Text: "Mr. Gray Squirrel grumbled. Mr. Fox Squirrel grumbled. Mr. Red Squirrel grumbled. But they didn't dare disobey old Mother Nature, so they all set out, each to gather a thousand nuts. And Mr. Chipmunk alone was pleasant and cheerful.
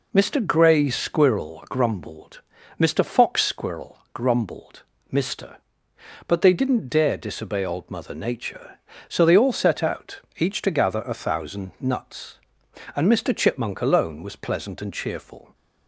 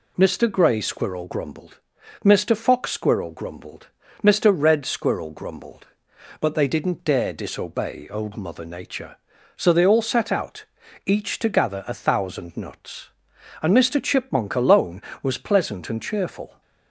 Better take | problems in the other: second | skips "Red Squirrel grumbled"; at 5.9 s

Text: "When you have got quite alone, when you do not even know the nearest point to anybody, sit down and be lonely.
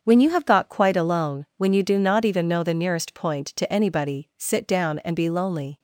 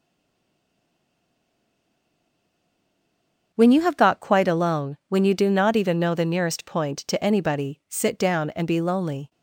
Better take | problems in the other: first | stays silent before the first word; strong; until 3.5 s; 3.5 s long // starts louder than the rest; strong; until 4.5 s; 7 dB; also in the first

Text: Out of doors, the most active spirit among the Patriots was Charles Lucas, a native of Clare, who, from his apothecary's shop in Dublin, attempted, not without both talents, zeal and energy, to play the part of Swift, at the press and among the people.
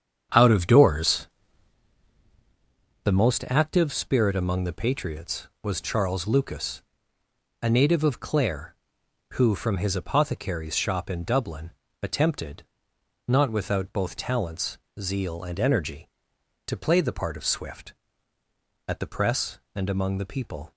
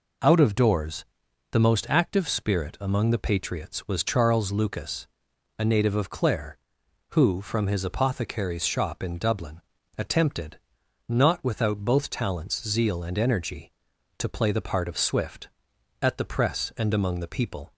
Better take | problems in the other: second | starts louder than the rest; strong; until 1.8 s; 8 dB

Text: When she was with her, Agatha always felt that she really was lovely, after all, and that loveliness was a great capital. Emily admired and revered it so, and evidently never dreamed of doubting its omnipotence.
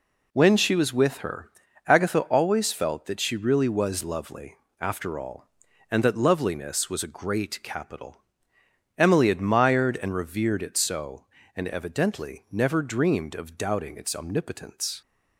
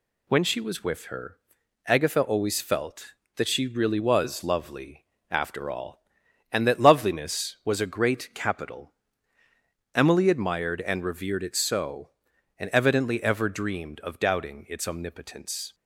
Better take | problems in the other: first | says "ever" for "never"; at 13.2 s

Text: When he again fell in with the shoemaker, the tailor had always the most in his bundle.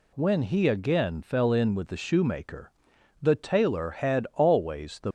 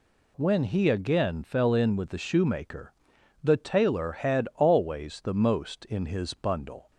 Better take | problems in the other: second | stops before "most in his bundle"; at 5.0 s

